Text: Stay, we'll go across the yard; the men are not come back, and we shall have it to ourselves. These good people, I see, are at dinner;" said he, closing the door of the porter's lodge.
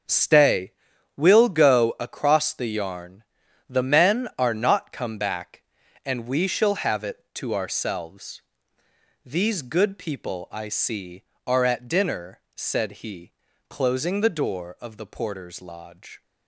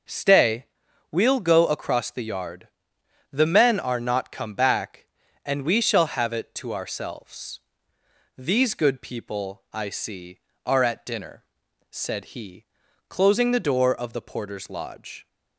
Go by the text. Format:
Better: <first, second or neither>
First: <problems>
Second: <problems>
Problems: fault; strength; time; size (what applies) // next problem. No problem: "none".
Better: second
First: starts louder than the rest; until 1.5 s; 7 dB // says "yarn" for "yard"; at 2.6 s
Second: starts louder than the rest; until 1.5 s; 6 dB